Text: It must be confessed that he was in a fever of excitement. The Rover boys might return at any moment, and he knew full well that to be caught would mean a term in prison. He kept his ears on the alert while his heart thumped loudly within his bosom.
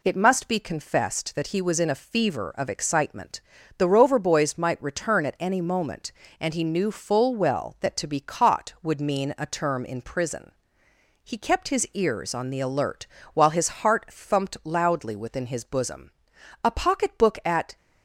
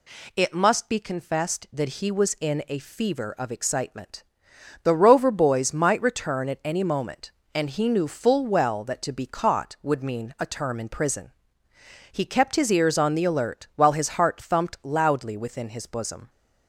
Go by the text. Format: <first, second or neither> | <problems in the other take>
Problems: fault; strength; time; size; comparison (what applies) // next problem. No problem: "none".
second | pauses between "alert" and "while"; slight; at 13.0 s; 0.28 s long // goes on to say "A pocketbook at"; noticeable; from 16.6 s on; 1.1 s long